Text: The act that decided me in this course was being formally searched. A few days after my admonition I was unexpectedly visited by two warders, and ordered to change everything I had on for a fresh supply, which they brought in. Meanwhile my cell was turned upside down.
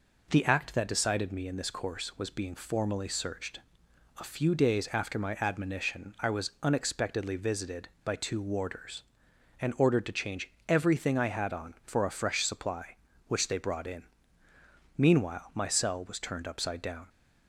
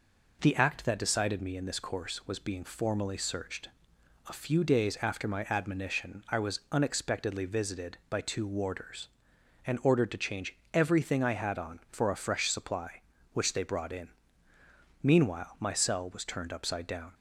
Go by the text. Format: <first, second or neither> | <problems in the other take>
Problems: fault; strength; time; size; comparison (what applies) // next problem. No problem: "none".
neither | pauses between "change" and "everything"; slight; the same in both